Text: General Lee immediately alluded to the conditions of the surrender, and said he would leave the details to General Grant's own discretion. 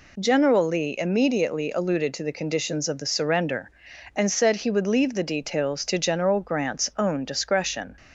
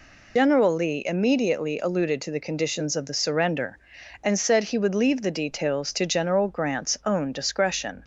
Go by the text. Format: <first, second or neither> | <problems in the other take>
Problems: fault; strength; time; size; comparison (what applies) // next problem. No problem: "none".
first | loses the start of "General"; at 0.3 s; 105 ms